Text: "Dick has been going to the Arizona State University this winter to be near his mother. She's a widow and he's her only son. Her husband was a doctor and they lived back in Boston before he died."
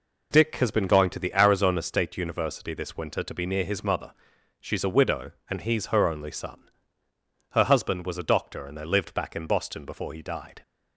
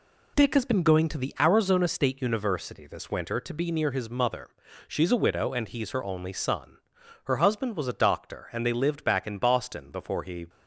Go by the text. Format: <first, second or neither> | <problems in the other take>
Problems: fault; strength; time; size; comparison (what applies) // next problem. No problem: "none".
first | stops before "died"; at 10.4 s